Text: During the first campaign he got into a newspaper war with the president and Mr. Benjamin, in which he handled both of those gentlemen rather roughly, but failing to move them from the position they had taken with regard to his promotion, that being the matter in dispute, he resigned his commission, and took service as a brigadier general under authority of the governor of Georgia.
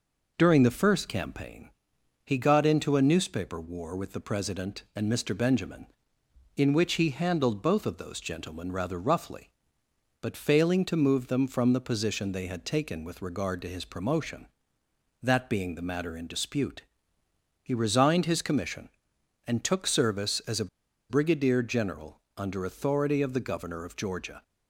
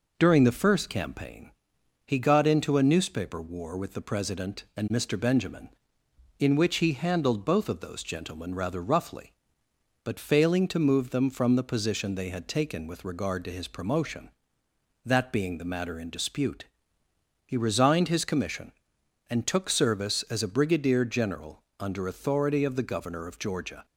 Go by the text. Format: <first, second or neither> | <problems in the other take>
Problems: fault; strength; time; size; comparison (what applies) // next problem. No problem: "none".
second | pauses between "campaign" and "he"; noticeable; at 1.7 s; 0.56 s long; noticeable in the second // pauses between "a" and "brigadier"; at 20.6 s; 0.41 s long // pauses between "general" and "under"; slight; at 22.1 s; 0.18 s long; slight in the second